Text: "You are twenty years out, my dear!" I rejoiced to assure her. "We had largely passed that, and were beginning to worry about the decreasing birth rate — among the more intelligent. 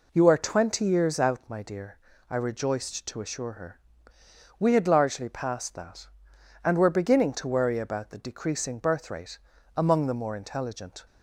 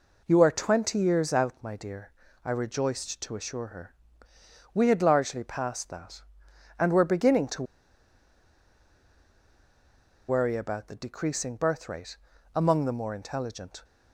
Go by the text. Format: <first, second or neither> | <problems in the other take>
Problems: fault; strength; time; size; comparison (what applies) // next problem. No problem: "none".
first | pauses between "to" and "worry"; strong; at 7.6 s; 2.6 s long